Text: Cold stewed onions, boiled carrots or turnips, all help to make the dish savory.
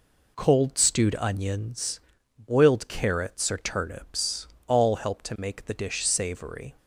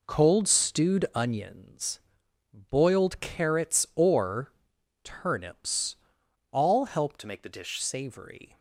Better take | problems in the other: first | pauses between "or" and "turnips"; noticeable; at 4.5 s; 0.54 s long // changes voice from "to" to "dish"; from 7.1 to 7.7 s; 0.6 s long

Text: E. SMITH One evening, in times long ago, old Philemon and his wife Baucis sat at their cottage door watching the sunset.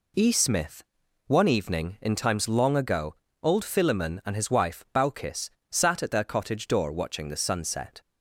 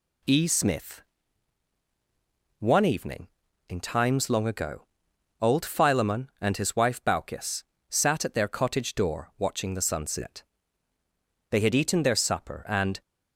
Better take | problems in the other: first | pauses between "SMITH" and "One"; strong; at 1.0 s; 1.5 s long; noticeable in the first // pauses between "Baucis" and "sat"; slight; at 7.6 s; 0.24 s long; slight in the first // goes on to say "They had eaten their supper and"; from 11.5 s on; 1.5 s long

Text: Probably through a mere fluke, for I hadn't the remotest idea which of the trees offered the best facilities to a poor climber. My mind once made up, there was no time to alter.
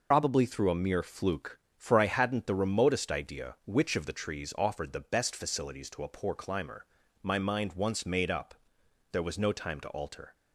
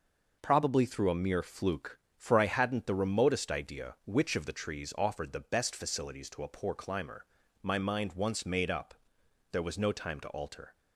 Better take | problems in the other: second | loses the start of "Probably"; at 0.1 s; 100 ms

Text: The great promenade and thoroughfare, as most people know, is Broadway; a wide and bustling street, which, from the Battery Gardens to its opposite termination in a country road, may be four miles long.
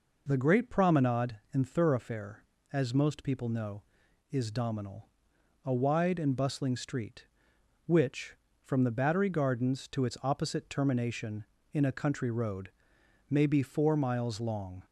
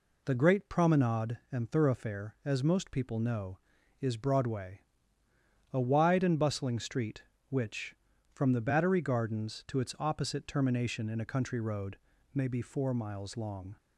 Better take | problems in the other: second | says "Dominal" for "Broadway"; at 4.5 s

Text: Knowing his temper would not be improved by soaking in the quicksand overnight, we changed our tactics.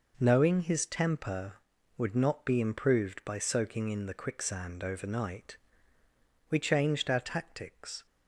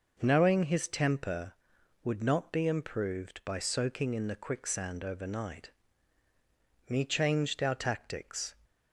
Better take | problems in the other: first | says "me" for "we"; at 6.8 s

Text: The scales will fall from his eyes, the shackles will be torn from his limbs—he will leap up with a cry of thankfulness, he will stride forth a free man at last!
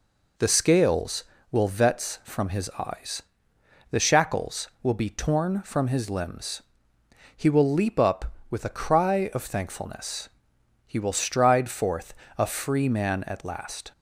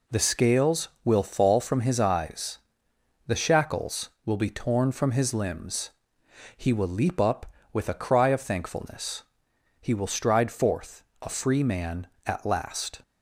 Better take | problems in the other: second | says "vets" for "fall"; at 1.6 s // pauses between "forth" and "a"; slight; at 12.1 s; 0.24 s long; slight in the second

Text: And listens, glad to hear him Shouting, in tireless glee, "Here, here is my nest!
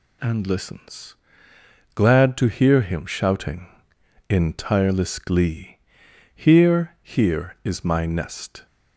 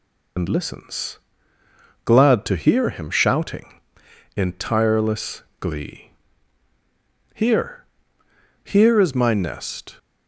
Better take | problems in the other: first | loses the start of "And"; at 0.3 s; 60 ms // pauses between "tireless" and "glee"; slight; at 5.4 s; 0.18 s long

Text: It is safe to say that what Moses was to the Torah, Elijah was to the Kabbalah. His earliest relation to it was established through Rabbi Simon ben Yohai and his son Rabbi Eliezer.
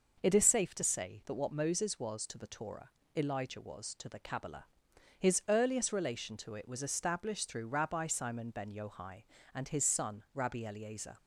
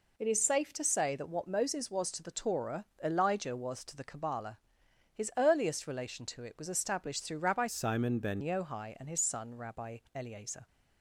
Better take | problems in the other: first | changes voice from "Simon" to "ben"; from 7.6 to 8.4 s; 0.8 s long // pauses between "Rabbi" and "Eliezer"; slight; at 9.9 s; 0.16 s long

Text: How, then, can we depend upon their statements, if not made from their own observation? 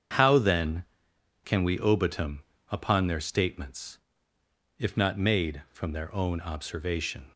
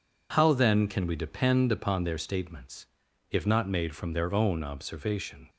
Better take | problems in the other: second | starts louder than the rest; until 1.8 s; 7 dB // says "obitum" for "depend"; at 1.7 s

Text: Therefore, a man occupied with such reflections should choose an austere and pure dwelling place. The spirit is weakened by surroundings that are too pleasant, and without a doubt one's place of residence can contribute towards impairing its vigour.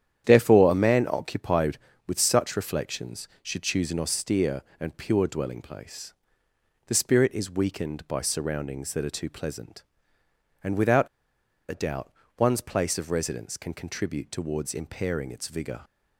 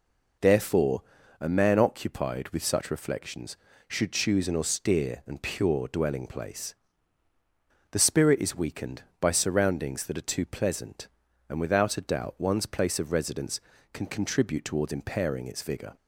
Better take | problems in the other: second | starts louder than the rest; strong; until 1.2 s; 10 dB // pauses between "without" and "a"; noticeable; at 11.0 s; 0.62 s long // pauses between "doubt" and "one's"; slight; at 12.1 s; 0.26 s long

